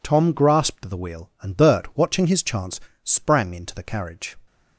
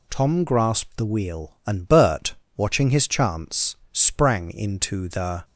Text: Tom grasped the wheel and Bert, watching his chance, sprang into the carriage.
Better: first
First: none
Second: stops before "carriage"; at 5.4 s

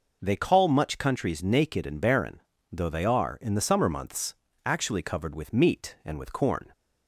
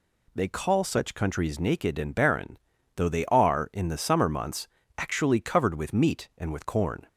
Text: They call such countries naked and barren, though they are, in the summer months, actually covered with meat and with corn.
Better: second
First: says "much" for "such"; at 0.6 s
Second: none

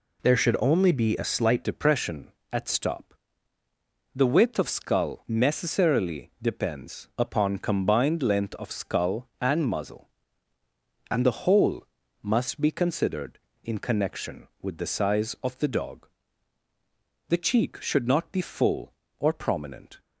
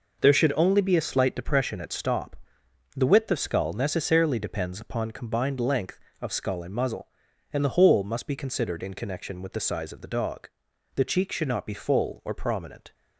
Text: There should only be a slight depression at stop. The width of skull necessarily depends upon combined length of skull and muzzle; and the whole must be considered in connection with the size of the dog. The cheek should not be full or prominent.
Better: second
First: changes voice at "depression"; from 1.6 s on; 18.3 s long // pauses between "whole" and "must"; slight; at 11.8 s; 0.36 s long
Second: none

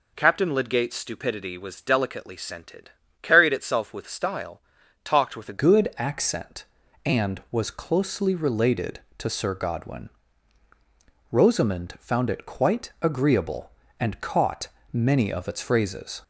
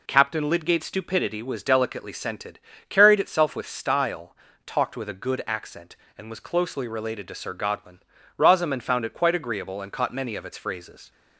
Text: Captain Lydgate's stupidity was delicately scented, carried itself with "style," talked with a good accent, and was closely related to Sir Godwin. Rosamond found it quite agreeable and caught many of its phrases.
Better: second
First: changes voice at "good"; from 5.5 s on; 10.7 s long // pauses between "caught" and "many"; slight; at 14.6 s; 0.24 s long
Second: none

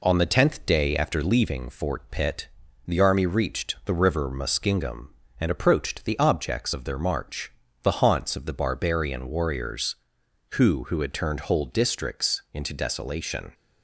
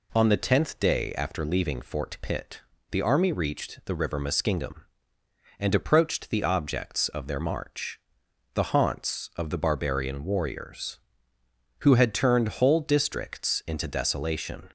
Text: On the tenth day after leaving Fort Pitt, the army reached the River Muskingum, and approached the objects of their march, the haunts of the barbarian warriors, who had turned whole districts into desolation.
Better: second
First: says "who" twice; at 10.8 s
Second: none

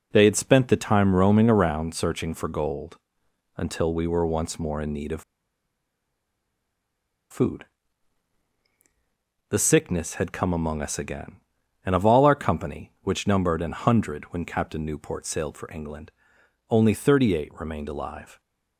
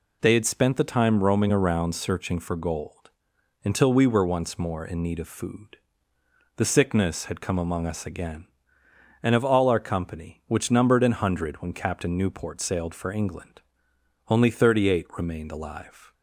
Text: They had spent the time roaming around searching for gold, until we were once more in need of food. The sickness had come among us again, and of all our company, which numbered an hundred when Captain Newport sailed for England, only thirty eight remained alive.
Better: second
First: pauses between "of" and "food"; strong; at 5.2 s; 2.0 s long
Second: none

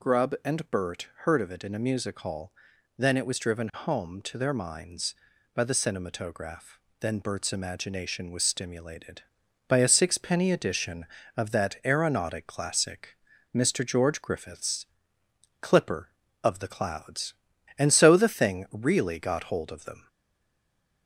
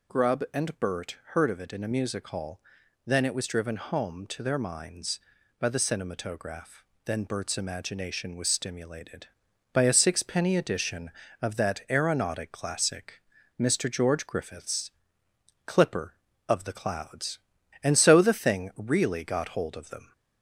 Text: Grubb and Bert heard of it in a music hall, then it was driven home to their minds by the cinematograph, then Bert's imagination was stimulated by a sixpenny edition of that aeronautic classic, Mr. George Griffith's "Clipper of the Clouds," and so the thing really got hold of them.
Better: second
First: pauses between "Bert" and "heard"; slight; at 1.0 s; 0.20 s long // pauses between "Griffith's" and "Clipper"; noticeable; at 14.8 s; 0.76 s long // stays silent after the last word; from 20.0 s on; 1.0 s long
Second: pauses between "Bert" and "heard"; slight; at 1.1 s; 0.20 s long // pauses between "Griffith's" and "Clipper"; noticeable; at 14.9 s; 0.76 s long

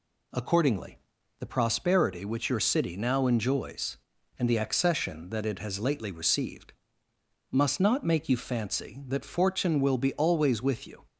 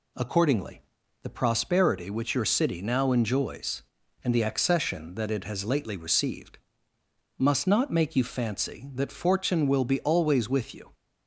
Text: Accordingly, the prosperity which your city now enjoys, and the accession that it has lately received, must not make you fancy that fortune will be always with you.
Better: neither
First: none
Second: none

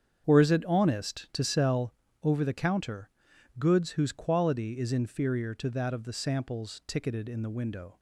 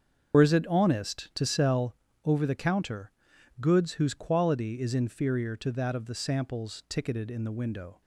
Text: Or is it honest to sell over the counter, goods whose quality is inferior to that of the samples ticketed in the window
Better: first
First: starts louder than the rest; strong; until 1.2 s; 8 dB // pauses between "sell" and "over"; slight; at 1.9 s; 0.30 s long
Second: loses the start of "Or"; at 0.3 s; 80 ms // starts louder than the rest; strong; until 1.3 s; 7.5 dB // pauses between "sell" and "over"; slight; at 1.9 s; 0.30 s long

